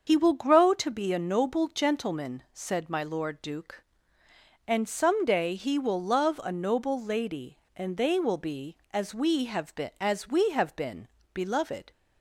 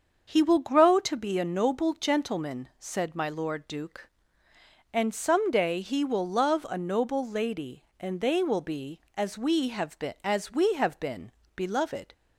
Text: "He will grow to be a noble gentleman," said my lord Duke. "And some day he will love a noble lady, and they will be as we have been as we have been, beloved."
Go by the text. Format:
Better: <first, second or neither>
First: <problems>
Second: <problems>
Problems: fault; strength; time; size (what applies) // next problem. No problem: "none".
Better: second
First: loses the start of "He"; at 0.0 s; 45 ms // starts louder than the rest; until 1.0 s; 6.5 dB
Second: starts louder than the rest; until 1.3 s; 6.5 dB